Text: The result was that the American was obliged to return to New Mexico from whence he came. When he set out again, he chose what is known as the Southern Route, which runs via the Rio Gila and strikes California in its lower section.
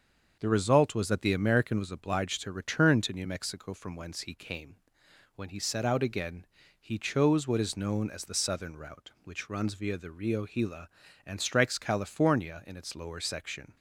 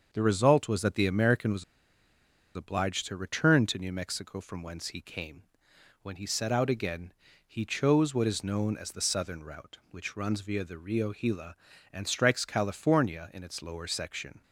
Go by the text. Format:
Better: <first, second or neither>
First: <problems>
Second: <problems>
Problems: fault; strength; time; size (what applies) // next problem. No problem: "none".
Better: first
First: starts louder than the rest; until 1.4 s; 6.5 dB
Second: starts louder than the rest; until 1.1 s; 6.5 dB // pauses between "was" and "obliged"; noticeable; at 1.6 s; 0.91 s long